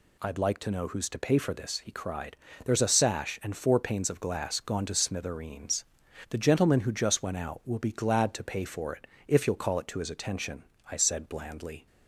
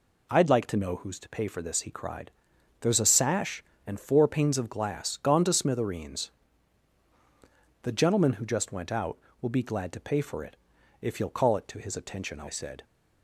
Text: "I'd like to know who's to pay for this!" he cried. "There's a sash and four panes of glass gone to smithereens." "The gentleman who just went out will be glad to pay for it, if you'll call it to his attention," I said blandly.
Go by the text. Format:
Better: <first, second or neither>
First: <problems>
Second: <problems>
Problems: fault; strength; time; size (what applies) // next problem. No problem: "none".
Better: first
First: none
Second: stops before "blandly"; at 12.8 s